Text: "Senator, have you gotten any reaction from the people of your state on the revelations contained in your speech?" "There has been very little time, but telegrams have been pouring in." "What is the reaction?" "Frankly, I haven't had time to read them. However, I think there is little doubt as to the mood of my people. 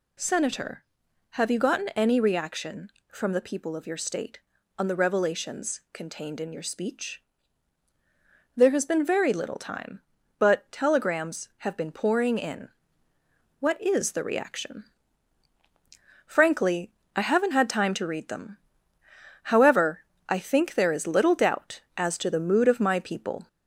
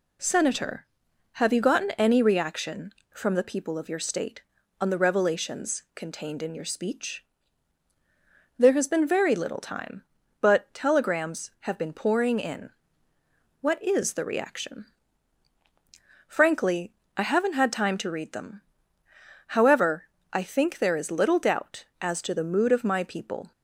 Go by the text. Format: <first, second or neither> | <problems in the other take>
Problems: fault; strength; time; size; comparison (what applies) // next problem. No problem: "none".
second | gets louder; slight; throughout; 2.5 dB